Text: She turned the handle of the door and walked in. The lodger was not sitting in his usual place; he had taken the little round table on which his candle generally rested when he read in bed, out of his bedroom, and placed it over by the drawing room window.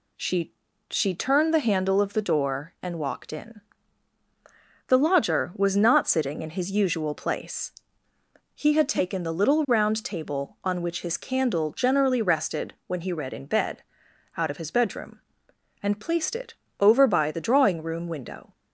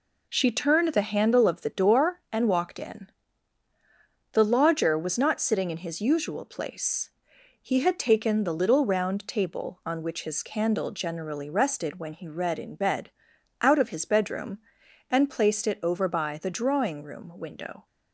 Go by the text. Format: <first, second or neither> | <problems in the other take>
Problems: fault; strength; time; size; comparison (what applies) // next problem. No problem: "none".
second | says "She" twice; at 0.8 s // pauses between "it" and "over"; slight; at 16.5 s; 0.28 s long